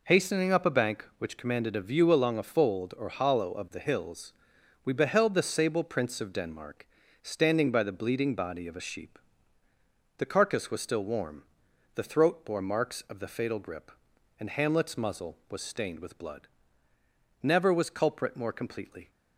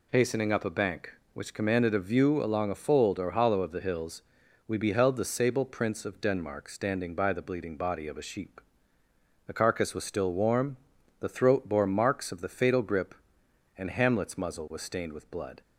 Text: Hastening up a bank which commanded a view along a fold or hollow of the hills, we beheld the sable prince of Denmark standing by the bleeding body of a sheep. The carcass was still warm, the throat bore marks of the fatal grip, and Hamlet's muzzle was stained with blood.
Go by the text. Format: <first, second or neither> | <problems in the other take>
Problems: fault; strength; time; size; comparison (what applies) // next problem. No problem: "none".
second | pauses between "Denmark" and "standing"; at 6.8 s; 0.38 s long // goes on to say "Never was culprit more completely"; strong; from 17.4 s on; 1.6 s long